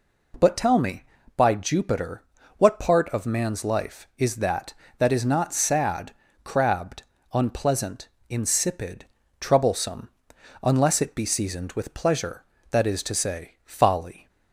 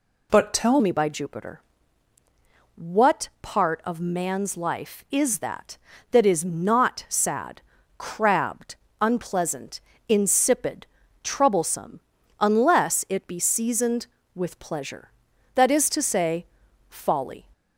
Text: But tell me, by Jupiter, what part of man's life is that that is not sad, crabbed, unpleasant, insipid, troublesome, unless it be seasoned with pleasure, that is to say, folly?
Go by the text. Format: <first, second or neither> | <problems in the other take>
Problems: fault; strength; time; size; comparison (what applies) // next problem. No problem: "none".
first | changes voice at "me"; from 0.8 s on; 16.6 s long